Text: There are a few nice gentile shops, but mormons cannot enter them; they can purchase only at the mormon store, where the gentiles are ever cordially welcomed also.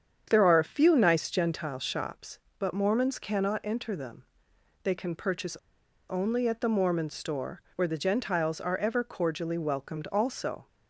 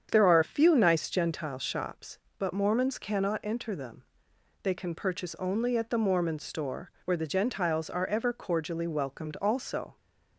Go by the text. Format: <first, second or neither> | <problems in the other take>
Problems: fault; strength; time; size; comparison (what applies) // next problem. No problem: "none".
second | starts louder than the rest; strong; until 1.3 s; 8 dB; strong in the second // pauses between "purchase" and "only"; noticeable; at 5.5 s; 0.52 s long